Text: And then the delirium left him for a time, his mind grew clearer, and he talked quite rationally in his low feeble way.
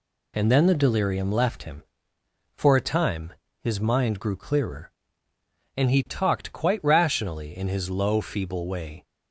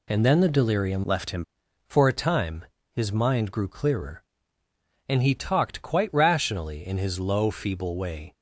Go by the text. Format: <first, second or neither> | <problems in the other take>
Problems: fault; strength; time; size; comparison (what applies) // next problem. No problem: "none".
first | changes voice from "left" to "him"; from 1.0 to 1.4 s; 0.4 s long